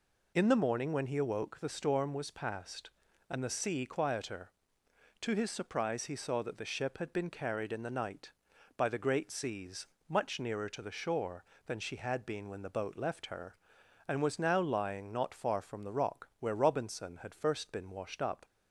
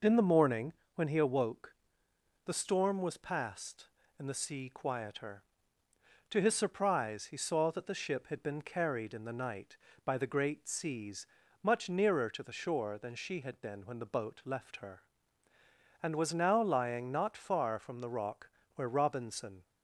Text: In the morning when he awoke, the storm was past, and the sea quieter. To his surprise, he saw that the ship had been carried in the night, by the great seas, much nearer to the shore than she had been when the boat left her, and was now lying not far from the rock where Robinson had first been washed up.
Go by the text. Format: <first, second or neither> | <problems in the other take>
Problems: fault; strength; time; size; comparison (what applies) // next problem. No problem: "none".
first | pauses between "morning" and "when"; slight; at 0.7 s; 0.22 s long // pauses between "rock" and "where"; slight; at 18.4 s; 0.26 s long // stops before "had first been washed up"; at 19.6 s